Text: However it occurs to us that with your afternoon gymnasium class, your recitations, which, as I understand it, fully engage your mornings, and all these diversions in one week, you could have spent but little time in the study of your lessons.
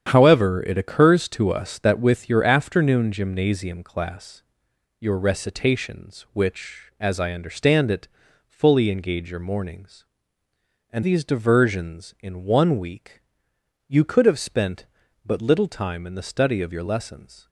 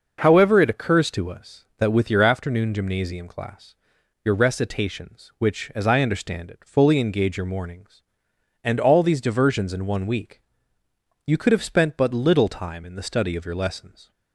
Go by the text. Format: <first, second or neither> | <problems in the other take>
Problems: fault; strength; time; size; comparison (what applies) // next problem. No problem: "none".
second | starts louder than the rest; strong; until 1.1 s; 9 dB // skips "all"; at 11.0 s